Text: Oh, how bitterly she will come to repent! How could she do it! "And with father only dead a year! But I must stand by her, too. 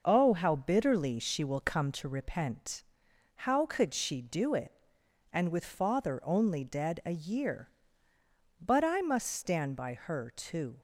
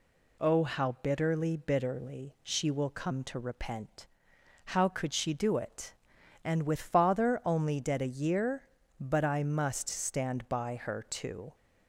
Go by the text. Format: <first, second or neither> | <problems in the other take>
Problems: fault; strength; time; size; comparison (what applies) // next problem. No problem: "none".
first | says "bitterly" twice; at 1.5 s